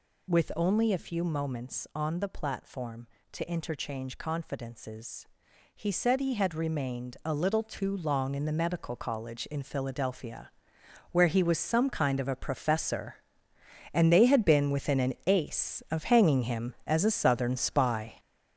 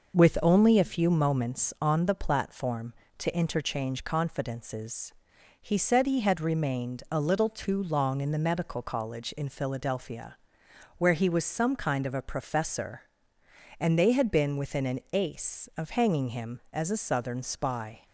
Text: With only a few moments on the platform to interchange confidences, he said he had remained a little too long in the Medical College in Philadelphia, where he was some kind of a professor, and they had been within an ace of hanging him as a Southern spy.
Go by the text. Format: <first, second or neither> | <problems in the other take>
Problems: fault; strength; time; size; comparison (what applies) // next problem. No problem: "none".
second | gets louder; throughout; 6.5 dB